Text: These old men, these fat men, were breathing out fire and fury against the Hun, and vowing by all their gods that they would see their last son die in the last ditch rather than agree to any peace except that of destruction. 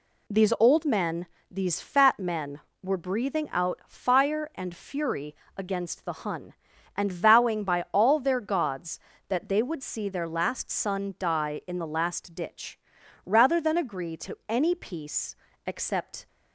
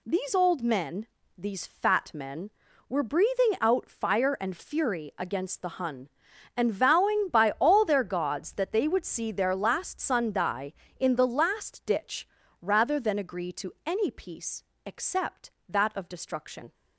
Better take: second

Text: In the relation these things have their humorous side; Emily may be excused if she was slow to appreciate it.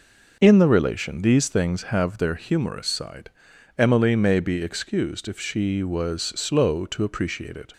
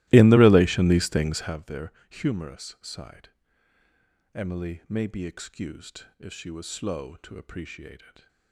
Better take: first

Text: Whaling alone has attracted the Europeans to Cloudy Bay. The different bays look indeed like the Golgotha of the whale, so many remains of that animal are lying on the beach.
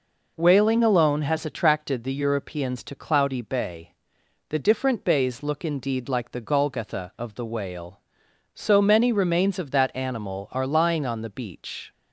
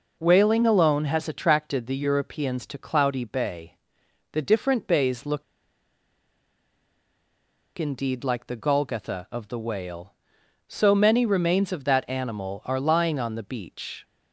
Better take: first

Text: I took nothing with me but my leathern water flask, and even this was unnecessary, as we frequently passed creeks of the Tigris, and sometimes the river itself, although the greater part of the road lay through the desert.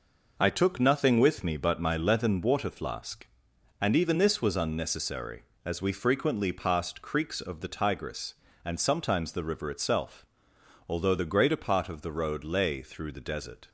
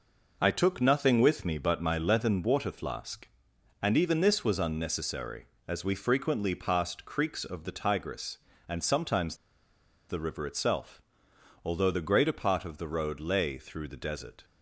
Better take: first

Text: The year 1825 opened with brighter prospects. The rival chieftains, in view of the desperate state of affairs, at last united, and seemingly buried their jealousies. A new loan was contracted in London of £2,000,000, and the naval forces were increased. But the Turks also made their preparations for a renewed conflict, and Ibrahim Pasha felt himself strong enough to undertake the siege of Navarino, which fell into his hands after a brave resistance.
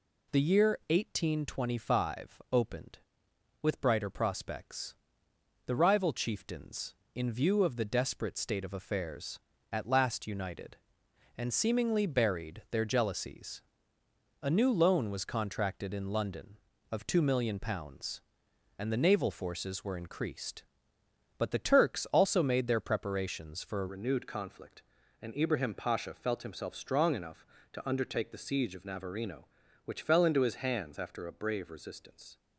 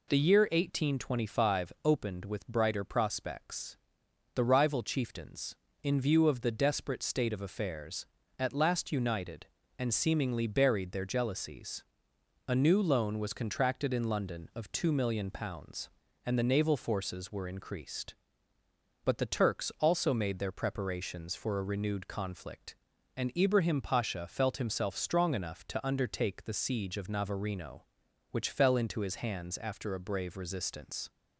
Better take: second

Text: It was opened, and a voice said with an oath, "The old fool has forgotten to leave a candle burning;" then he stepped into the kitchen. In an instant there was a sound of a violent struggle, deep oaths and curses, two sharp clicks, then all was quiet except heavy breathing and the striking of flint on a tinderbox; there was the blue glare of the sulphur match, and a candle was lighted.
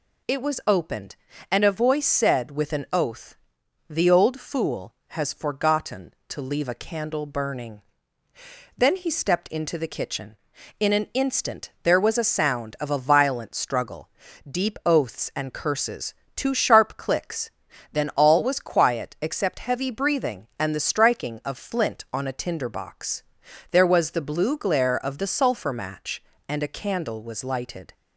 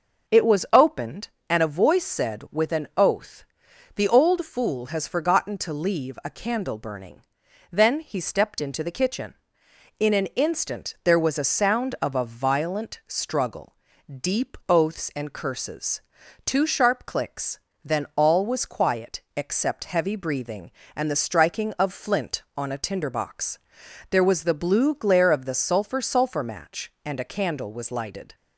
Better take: first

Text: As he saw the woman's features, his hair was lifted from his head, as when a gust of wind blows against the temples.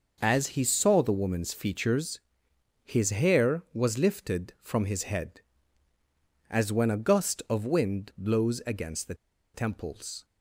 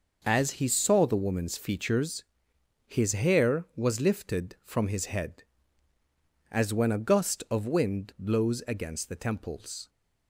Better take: second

